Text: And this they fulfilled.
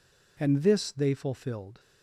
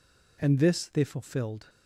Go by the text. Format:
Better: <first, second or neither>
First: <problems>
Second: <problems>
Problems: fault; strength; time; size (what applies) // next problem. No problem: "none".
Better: neither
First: none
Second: none